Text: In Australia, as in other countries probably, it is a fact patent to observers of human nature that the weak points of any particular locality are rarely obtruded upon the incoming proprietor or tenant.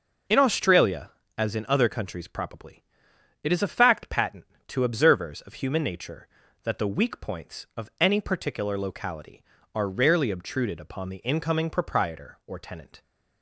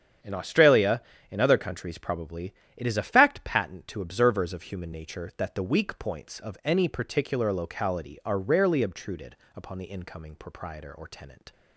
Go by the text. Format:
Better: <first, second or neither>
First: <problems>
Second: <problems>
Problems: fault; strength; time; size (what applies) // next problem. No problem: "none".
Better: first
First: none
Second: starts louder than the rest; strong; until 1.5 s; 8.5 dB // skips "as"; at 1.1 s // pauses between "obtruded" and "upon"; slight; at 9.3 s; 0.20 s long